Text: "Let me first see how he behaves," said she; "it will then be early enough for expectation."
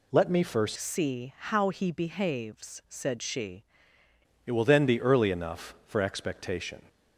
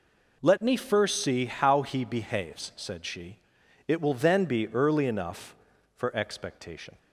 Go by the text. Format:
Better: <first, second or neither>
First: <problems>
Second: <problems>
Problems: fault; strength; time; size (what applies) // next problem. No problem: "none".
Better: second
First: changes voice from "see" to "she"; from 0.7 to 3.6 s; 2.9 s long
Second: none